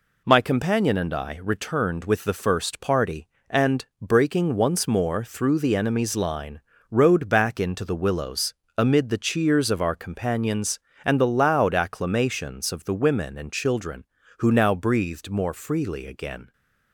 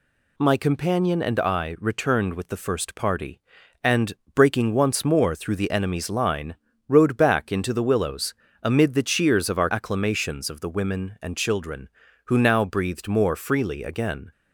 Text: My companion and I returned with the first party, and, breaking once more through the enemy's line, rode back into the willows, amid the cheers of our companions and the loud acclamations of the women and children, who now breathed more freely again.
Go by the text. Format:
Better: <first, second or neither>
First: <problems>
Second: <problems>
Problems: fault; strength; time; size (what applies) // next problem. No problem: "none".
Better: first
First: none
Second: skips "companions and the loud"; at 9.7 s